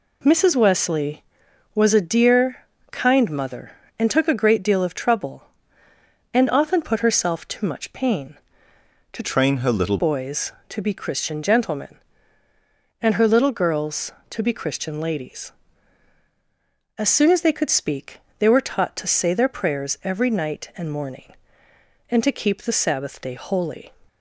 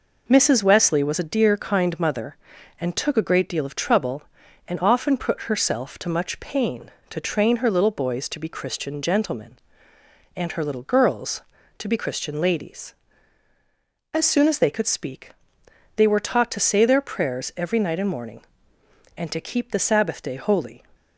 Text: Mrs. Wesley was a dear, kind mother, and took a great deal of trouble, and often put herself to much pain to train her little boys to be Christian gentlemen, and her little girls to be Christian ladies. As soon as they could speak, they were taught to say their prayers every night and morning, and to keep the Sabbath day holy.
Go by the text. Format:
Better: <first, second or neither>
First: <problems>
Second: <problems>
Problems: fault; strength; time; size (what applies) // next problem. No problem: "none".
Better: second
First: changes voice from "train" to "little"; from 9.2 to 9.9 s; 0.7 s long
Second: none